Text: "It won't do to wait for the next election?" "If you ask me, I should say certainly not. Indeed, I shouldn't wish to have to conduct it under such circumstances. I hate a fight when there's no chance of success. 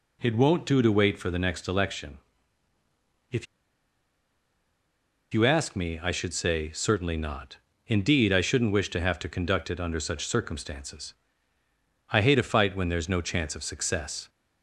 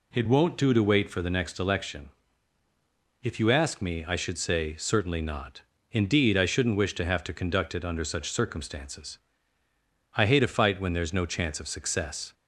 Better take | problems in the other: second | pauses between "If" and "you"; strong; at 3.4 s; 1.8 s long

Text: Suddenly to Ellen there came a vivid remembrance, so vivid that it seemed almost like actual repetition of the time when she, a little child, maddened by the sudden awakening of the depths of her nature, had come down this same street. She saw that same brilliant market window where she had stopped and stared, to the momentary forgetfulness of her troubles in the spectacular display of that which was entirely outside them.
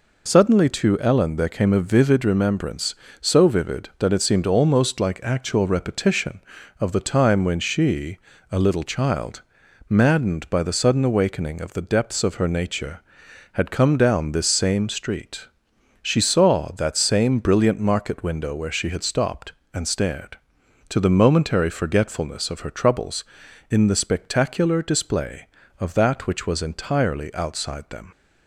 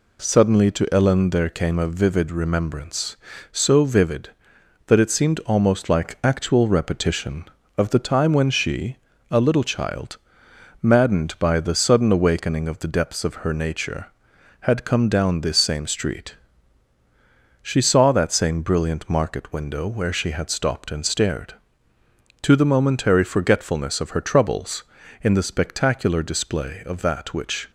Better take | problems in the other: first | stops before "was entirely outside them"; at 27.6 s

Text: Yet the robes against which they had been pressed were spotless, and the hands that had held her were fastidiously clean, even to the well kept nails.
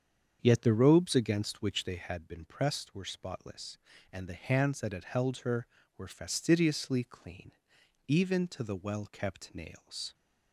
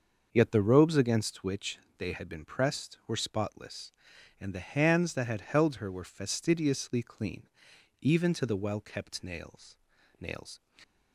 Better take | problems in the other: first | starts louder than the rest; until 1.3 s; 6.5 dB; strong in the first // pauses between "which" and "they"; slight; at 1.7 s; 0.20 s long // says "nails" twice; at 10.2 s

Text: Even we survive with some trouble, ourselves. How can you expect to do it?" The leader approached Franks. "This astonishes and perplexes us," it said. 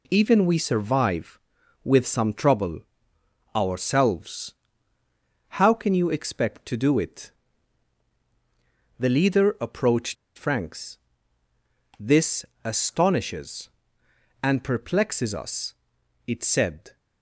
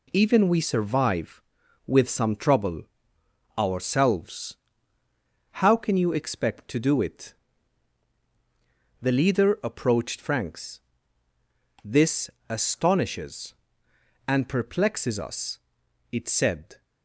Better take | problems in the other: second | pauses between "approached" and "Franks"; slight; at 10.1 s; 0.22 s long // pauses between "This" and "astonishes"; slight; at 12.4 s; 0.20 s long; slight in the second

